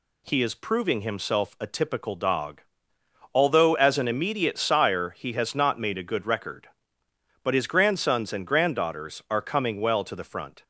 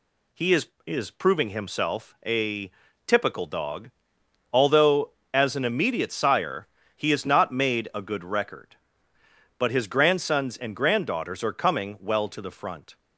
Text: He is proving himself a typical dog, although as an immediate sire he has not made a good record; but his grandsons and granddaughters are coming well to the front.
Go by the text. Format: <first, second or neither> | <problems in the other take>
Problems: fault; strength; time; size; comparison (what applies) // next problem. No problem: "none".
first | says "is" twice; at 0.8 s // pauses between "a" and "typical"; slight; at 2.7 s; 0.36 s long // pauses between "sire" and "he"; slight; at 6.6 s; 0.28 s long